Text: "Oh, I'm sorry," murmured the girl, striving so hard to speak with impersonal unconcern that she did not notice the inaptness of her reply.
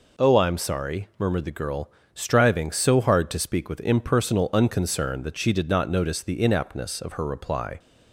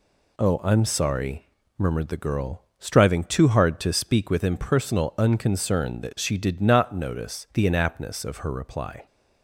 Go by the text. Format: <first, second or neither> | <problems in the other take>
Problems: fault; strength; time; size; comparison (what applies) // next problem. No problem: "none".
first | says "too" for "so"; at 3.2 s